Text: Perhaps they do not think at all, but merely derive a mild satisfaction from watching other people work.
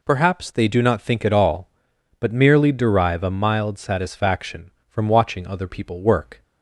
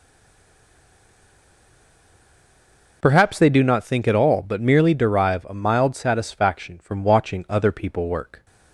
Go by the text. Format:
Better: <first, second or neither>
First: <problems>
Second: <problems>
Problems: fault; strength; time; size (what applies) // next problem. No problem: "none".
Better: first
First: none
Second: stays silent before the first word; strong; until 3.0 s; 3.0 s long